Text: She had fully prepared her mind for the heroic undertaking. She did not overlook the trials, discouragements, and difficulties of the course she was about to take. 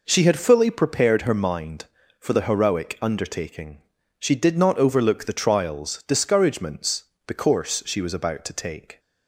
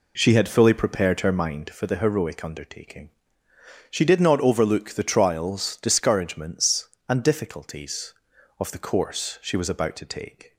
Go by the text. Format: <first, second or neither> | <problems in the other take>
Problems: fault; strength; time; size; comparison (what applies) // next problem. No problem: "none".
second | skips "and difficulties of"; at 7.1 s